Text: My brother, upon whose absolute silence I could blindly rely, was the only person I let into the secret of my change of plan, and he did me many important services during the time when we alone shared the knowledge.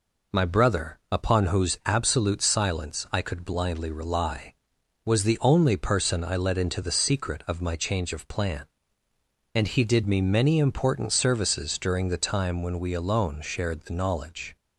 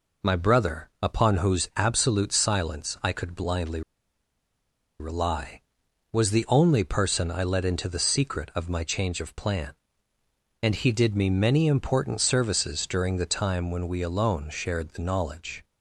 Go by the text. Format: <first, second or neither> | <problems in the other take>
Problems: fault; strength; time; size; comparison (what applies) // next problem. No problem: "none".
first | pauses between "blindly" and "rely"; at 3.8 s; 1.1 s long